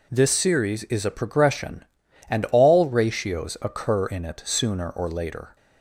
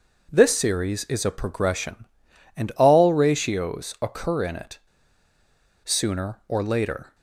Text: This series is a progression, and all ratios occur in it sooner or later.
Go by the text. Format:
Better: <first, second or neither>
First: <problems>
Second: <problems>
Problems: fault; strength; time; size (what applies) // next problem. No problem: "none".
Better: first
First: none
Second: pauses between "it" and "sooner"; at 4.7 s; 1.0 s long